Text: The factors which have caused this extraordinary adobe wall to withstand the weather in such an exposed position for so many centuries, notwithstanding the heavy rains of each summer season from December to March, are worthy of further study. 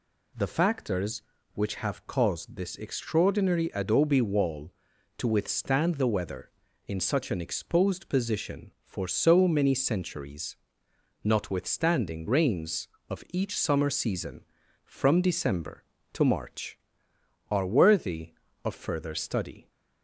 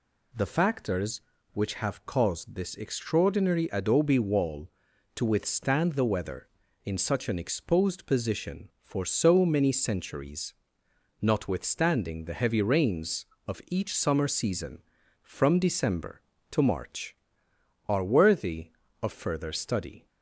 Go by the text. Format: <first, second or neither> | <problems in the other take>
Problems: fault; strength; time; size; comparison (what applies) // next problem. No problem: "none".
second | skips "the heavy"; at 12.2 s